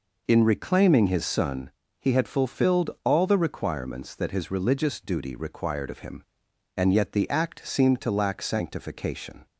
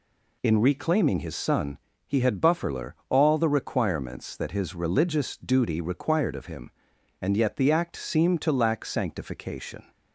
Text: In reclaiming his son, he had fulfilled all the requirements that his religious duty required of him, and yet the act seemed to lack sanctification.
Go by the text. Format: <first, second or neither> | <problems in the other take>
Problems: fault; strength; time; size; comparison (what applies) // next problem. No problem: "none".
first | says "bufferler" for "fulfilled"; at 2.4 s